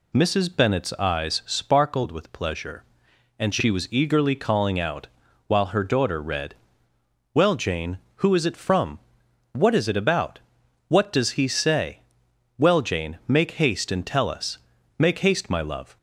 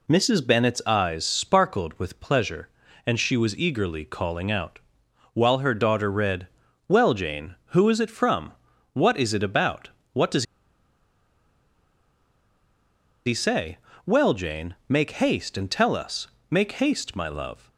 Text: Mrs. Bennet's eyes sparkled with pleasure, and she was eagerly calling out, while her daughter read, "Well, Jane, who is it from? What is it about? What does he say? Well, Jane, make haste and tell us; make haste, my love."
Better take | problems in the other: first | pauses between "does" and "he"; strong; at 10.4 s; 2.8 s long

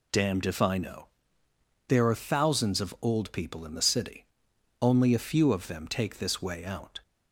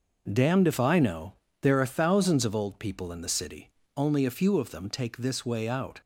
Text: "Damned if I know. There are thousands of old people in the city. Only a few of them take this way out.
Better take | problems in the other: neither | none

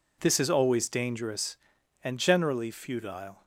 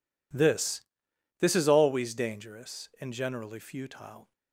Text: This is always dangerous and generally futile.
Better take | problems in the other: first | says "This" twice; at 1.3 s

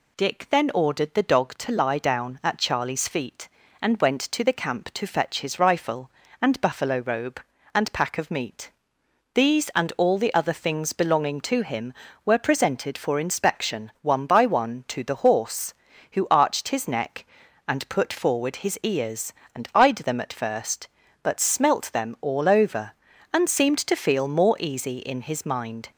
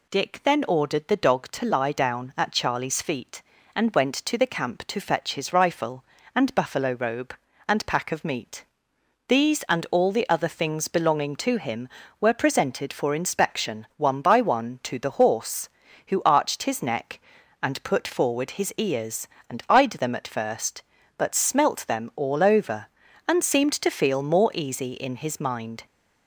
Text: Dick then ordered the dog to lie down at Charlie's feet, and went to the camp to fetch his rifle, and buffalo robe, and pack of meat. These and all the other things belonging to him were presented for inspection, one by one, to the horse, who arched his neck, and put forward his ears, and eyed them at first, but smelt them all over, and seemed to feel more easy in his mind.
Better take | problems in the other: neither | none

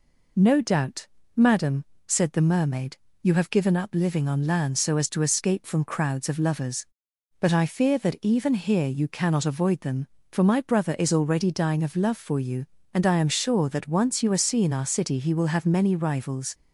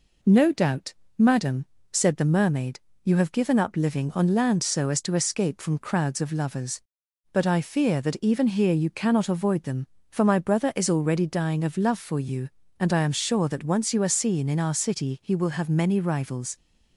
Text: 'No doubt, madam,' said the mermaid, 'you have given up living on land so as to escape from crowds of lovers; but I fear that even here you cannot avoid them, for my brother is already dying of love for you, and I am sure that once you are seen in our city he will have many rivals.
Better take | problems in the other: second | skips "in"; at 14.7 s

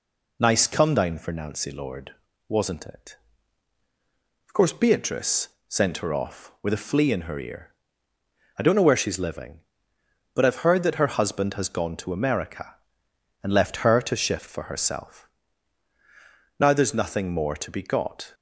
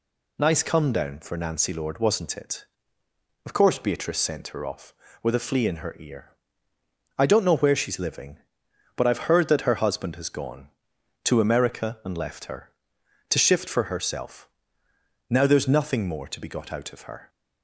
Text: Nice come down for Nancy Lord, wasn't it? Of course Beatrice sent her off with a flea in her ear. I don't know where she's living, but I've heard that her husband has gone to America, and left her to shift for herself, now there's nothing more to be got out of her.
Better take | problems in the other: second | pauses between "Beatrice" and "sent"; slight; at 5.4 s; 0.18 s long // stops before "out of her"; at 18.3 s

